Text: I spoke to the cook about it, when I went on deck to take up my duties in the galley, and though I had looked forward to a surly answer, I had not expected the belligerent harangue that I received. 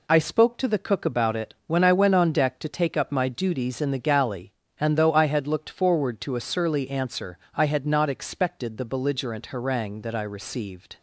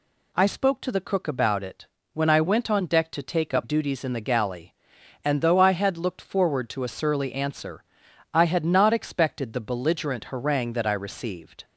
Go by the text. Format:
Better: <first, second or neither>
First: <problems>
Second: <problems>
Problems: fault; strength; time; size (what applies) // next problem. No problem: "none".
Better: first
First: none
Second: skips "my"; at 3.6 s